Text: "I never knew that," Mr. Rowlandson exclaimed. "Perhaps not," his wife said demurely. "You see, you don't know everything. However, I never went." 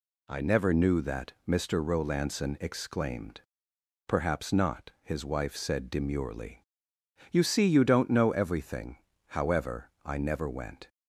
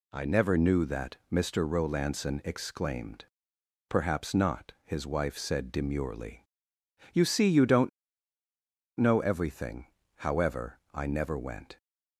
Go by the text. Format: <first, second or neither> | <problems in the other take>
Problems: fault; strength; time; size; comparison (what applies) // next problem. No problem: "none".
first | pauses between "don't" and "know"; at 7.8 s; 1.0 s long